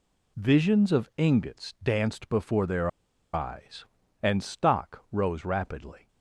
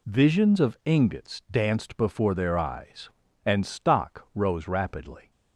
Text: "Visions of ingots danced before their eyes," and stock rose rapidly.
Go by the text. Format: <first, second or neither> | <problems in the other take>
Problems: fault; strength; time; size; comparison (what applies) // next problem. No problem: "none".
second | pauses between "their" and "eyes"; at 2.8 s; 0.43 s long